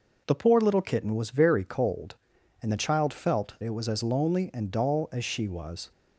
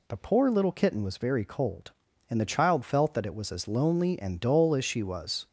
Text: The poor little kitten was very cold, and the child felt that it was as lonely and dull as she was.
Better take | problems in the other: second | skips "that"; at 3.5 s

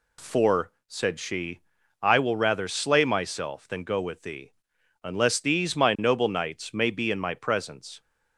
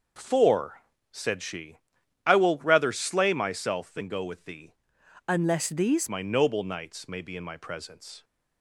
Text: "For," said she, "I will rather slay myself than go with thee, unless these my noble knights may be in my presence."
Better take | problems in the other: first | changes voice from "unless" to "these"; from 5.2 to 6.0 s; 0.8 s long

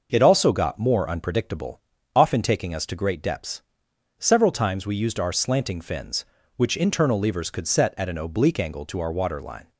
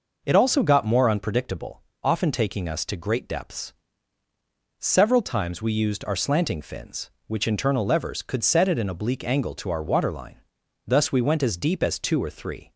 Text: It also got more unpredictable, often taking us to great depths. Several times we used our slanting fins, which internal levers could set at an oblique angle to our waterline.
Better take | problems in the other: first | goes on to say "Thus we went as deep as two or three"; strong; from 10.8 s on; 1.8 s long

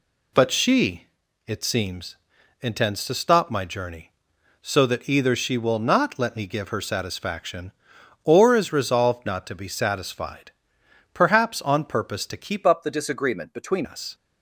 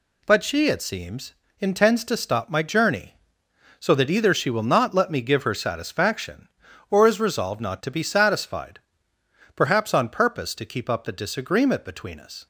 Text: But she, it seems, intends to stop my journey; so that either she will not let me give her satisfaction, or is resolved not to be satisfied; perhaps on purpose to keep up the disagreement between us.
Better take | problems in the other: second | changes voice from "up" to "between"; from 12.6 to 13.8 s; 1.2 s long

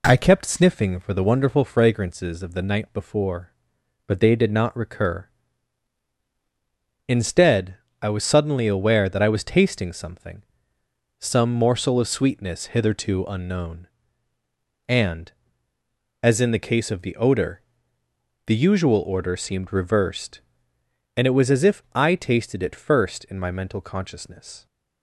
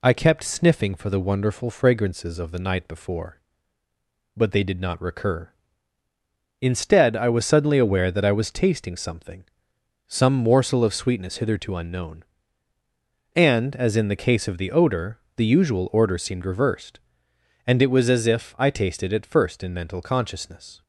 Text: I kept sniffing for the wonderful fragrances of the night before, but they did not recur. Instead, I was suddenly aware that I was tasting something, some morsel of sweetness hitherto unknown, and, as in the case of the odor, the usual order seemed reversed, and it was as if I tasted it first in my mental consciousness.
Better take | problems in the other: first | skips "my"; at 19.7 s

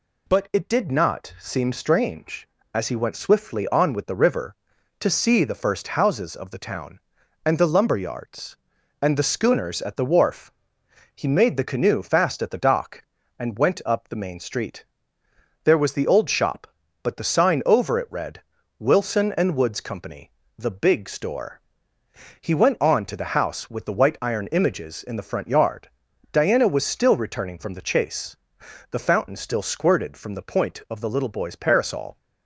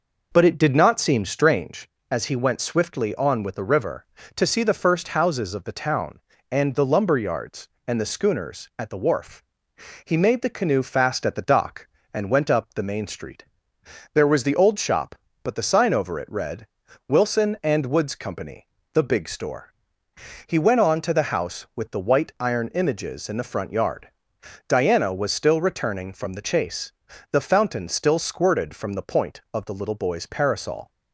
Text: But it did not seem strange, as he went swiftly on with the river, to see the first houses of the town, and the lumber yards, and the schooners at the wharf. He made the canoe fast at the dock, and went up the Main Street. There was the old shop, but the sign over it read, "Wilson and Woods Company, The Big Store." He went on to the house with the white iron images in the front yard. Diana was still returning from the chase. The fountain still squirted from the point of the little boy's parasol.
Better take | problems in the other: first | starts louder than the rest; noticeable; until 2.0 s; 5.5 dB

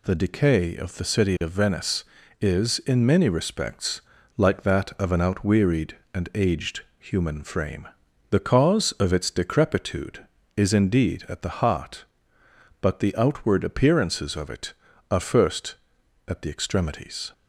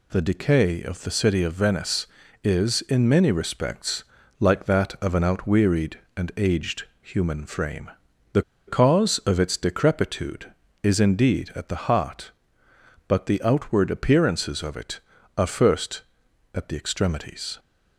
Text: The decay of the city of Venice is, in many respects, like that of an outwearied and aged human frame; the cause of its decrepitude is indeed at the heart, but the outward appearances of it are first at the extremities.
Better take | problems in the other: first | pauses between "aged" and "human"; slight; at 6.8 s; 0.18 s long; slight in the first // pauses between "the" and "cause"; slight; at 8.4 s; 0.26 s long

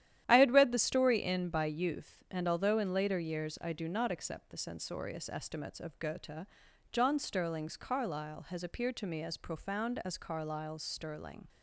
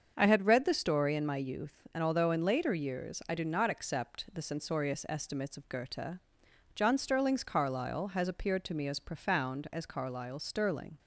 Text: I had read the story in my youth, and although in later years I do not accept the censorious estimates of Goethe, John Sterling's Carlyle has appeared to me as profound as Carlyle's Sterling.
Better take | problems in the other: second | starts louder than the rest; strong; until 1.2 s; 11 dB; also in the second // says "by" for "my"; at 1.5 s

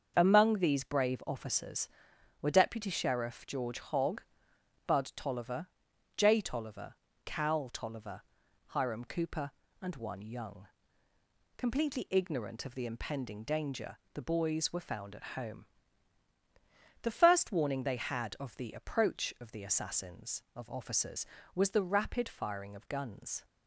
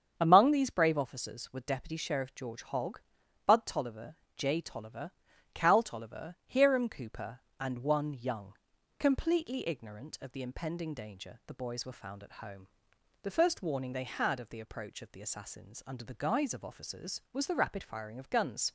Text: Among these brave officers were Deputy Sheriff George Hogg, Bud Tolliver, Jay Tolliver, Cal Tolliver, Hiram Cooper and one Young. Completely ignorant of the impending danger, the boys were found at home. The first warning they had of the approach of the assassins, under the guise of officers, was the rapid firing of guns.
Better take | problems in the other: second | starts louder than the rest; until 1.1 s; 6.5 dB; strong in the second // skips "under the guise"; at 20.4 s

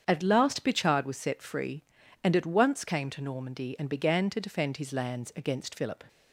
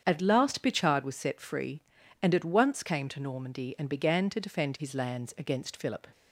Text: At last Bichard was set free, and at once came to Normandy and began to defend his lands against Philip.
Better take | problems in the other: neither | starts louder than the rest; strong; the same in both

